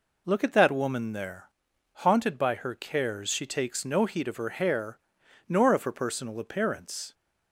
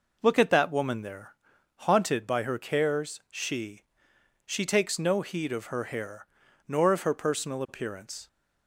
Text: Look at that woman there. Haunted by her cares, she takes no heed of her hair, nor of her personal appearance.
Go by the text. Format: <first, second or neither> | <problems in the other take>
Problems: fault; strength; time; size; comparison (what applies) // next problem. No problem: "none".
first | says "she" twice; at 4.4 s